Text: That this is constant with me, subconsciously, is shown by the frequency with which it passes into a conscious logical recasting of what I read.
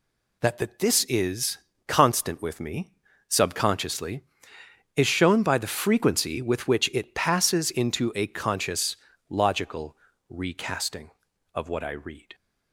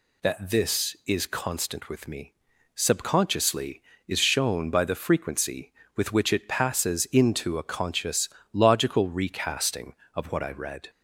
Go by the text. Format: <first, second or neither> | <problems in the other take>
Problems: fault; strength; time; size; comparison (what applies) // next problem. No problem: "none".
second | says "That" twice; at 0.5 s // pauses between "is" and "constant"; slight; at 1.5 s; 0.30 s long // pauses between "conscious" and "logical"; slight; at 8.9 s; 0.32 s long; slight in the second // pauses between "logical" and "recasting"; slight; at 9.9 s; 0.32 s long